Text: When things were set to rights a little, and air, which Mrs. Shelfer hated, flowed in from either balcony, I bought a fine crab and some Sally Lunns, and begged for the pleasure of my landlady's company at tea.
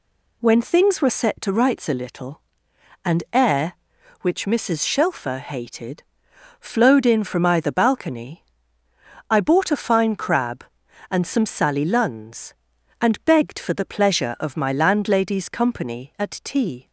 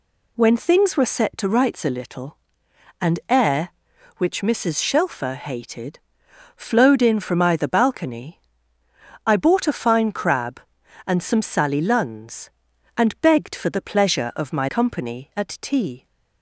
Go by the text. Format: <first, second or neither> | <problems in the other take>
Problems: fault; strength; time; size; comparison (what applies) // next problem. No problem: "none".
first | skips "landlady's"; at 14.6 s